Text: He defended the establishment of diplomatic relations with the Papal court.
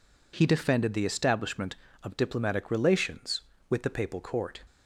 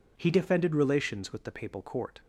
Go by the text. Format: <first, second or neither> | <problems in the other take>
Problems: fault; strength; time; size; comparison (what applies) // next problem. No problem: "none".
first | skips "the establishment of diplomatic"; at 0.7 s